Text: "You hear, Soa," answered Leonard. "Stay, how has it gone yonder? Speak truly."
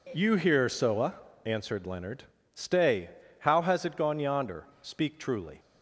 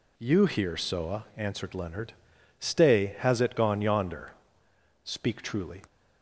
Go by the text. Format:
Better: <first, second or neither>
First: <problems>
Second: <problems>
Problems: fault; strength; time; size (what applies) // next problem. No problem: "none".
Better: first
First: none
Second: skips "how"; at 3.1 s